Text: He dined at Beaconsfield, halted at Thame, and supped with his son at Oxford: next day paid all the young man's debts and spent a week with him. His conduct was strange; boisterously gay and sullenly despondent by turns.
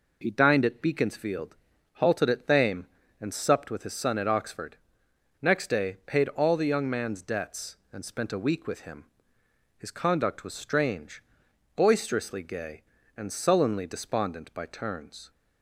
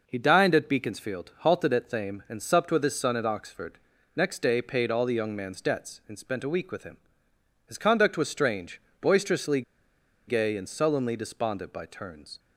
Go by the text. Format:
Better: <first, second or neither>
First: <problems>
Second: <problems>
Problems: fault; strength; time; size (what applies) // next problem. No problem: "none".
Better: first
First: none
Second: pauses between "boisterously" and "gay"; noticeable; at 9.6 s; 0.66 s long